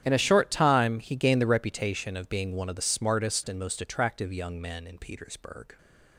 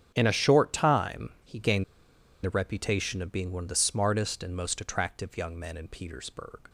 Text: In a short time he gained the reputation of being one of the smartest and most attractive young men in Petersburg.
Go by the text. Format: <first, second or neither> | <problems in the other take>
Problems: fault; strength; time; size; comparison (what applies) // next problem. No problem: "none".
first | starts louder than the rest; strong; until 1.1 s; 9.5 dB; strong in the first // pauses between "gained" and "the"; noticeable; at 1.8 s; 0.61 s long